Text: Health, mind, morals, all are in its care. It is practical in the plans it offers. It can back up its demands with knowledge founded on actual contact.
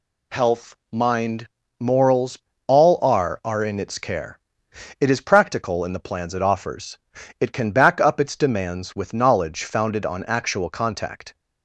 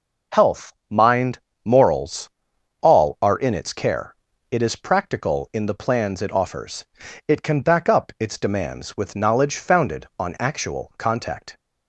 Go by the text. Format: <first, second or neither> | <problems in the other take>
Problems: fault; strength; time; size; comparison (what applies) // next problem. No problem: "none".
second | says "are" twice; at 3.4 s